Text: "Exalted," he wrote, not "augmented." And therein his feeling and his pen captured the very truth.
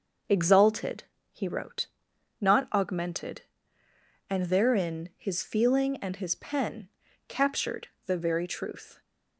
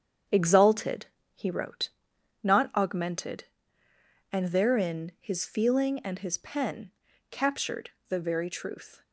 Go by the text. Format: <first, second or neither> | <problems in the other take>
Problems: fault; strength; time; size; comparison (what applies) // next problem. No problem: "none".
first | gets quieter; strong; throughout; 7 dB // starts louder than the rest; strong; until 1.6 s; 8 dB; noticeable in the first // pauses between "pen" and "captured"; at 6.9 s; 0.38 s long; also in the first // pauses between "captured" and "the"; slight; at 7.9 s; 0.18 s long; slight in the first